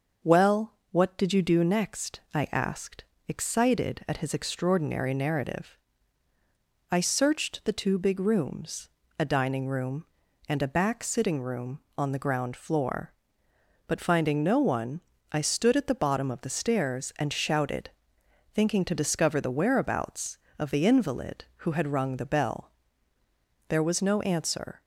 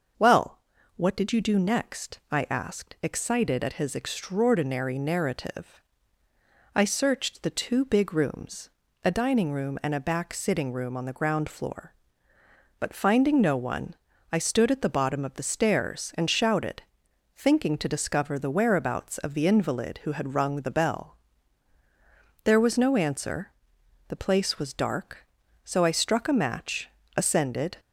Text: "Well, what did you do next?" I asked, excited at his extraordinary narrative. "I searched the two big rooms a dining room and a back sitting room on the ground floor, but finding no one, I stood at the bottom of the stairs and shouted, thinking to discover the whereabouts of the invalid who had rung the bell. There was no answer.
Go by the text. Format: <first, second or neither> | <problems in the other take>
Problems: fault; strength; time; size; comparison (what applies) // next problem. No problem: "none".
first | starts louder than the rest; noticeable; until 1.5 s; 6 dB; noticeable in the first // pauses between "rooms" and "a"; slight; at 8.6 s; 0.36 s long; slight in the first // goes on to say "The place was dark so I struck a match ascended"; strong; from 24.0 s on; 3.7 s long